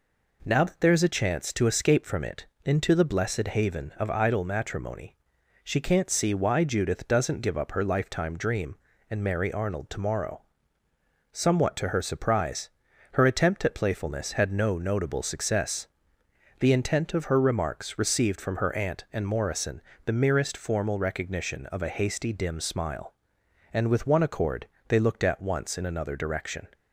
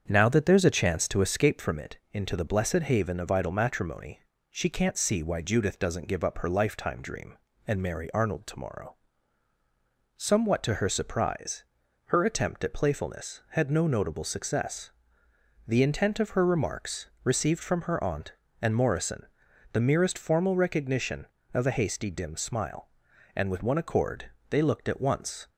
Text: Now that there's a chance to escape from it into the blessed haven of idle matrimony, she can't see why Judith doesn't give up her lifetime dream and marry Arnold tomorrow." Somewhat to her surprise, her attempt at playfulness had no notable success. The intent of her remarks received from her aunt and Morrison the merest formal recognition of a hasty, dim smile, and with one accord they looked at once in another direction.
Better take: first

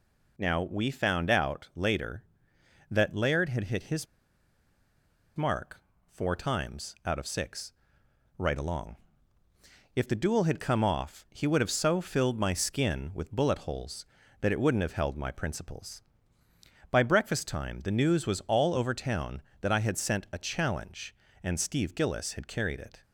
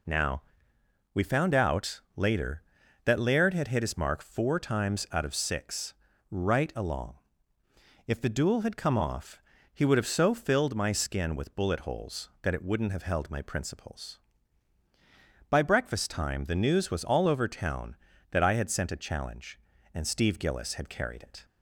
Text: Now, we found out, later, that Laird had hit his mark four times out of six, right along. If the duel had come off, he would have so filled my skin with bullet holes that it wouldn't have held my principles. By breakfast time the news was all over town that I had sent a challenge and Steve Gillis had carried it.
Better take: second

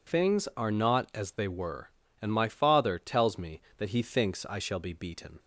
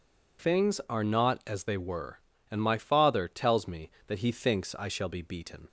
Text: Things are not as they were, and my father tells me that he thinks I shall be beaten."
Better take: neither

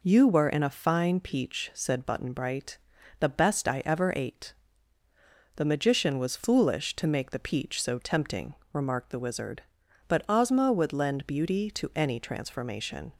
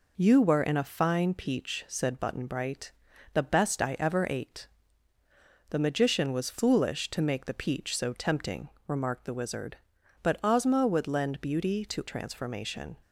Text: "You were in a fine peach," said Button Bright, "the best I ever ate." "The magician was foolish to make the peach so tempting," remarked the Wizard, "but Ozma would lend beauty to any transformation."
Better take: first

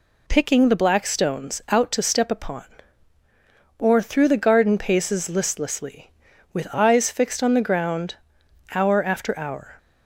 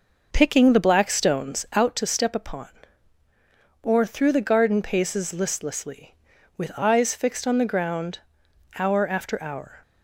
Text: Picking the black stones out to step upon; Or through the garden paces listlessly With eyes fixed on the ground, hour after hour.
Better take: first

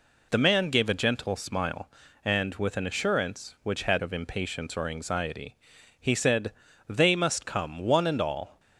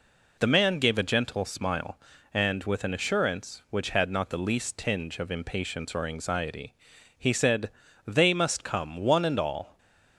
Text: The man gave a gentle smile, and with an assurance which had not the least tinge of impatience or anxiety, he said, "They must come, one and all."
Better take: second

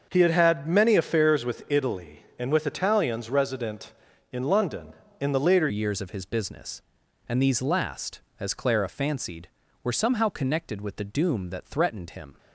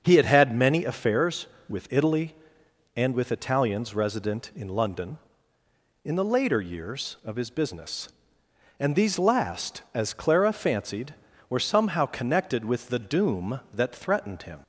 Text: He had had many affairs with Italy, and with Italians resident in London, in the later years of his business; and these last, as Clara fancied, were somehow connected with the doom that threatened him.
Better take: second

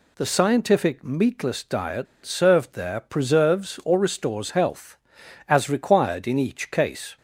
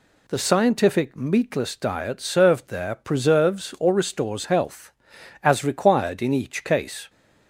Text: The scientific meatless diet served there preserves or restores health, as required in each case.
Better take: second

